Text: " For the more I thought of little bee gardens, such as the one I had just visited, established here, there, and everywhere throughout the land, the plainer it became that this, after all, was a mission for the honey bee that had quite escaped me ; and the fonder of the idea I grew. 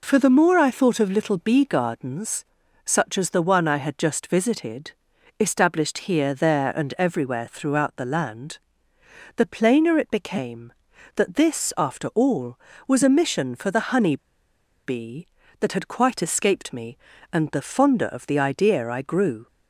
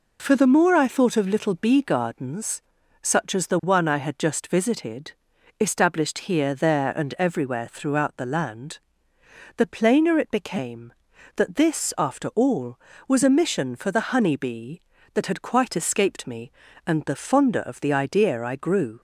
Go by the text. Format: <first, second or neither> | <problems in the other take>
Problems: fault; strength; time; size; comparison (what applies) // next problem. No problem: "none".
second | pauses between "honey" and "bee"; noticeable; at 14.1 s; 0.69 s long